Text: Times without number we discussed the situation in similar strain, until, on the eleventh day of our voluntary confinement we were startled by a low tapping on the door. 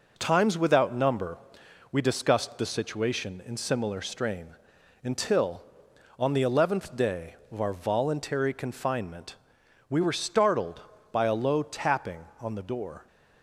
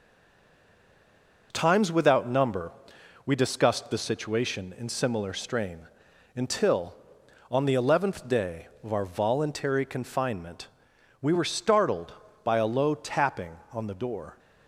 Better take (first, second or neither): first